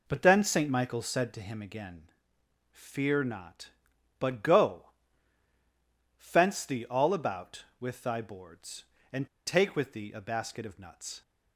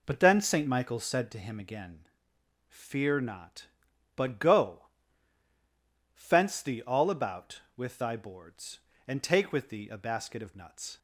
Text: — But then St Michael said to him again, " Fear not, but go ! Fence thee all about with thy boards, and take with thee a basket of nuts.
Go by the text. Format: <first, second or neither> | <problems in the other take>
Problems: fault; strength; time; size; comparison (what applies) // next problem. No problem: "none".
second | pauses between "and" and "take"; slight; at 9.2 s; 0.19 s long